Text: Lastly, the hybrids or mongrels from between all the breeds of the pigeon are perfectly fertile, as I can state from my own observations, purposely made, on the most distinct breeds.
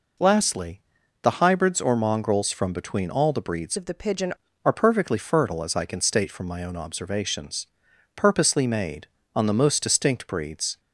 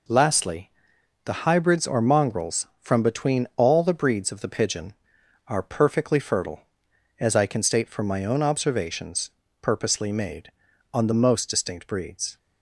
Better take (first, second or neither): second